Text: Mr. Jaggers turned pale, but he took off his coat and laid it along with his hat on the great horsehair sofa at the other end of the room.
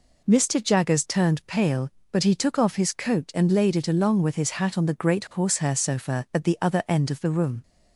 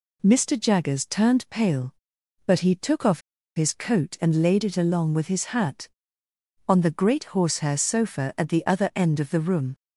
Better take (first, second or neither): first